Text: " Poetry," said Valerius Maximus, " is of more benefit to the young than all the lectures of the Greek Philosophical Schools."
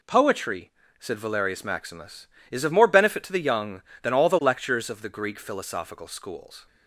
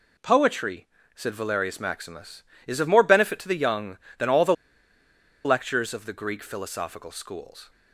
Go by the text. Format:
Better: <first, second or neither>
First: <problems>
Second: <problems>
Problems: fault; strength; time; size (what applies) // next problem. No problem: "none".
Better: first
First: none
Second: pauses between "the" and "lectures"; noticeable; at 4.5 s; 0.92 s long